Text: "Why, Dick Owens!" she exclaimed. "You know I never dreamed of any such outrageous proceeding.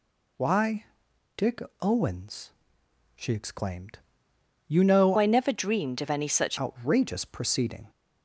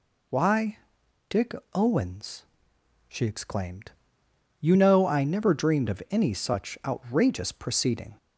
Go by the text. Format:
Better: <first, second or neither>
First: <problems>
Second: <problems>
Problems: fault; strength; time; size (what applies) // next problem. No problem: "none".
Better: second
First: pauses between "Dick" and "Owens"; slight; at 1.6 s; 0.20 s long // changes voice from "I" to "such"; from 5.1 to 6.5 s; 1.4 s long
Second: pauses between "Dick" and "Owens"; slight; at 1.5 s; 0.20 s long